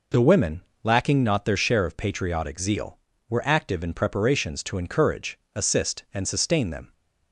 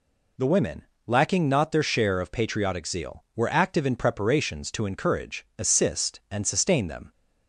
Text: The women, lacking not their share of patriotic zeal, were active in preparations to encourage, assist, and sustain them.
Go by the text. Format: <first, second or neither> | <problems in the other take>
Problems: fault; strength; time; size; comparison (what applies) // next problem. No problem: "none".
neither | none